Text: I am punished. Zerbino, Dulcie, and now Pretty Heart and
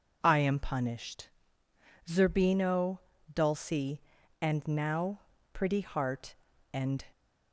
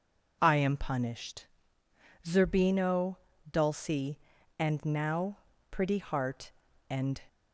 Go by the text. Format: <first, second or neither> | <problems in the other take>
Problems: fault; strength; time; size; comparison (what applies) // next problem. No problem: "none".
neither | pauses between "now" and "Pretty"; slight; the same in both